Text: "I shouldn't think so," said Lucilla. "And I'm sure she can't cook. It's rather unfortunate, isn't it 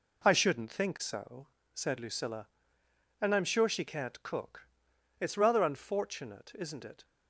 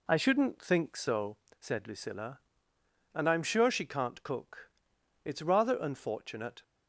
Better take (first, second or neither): first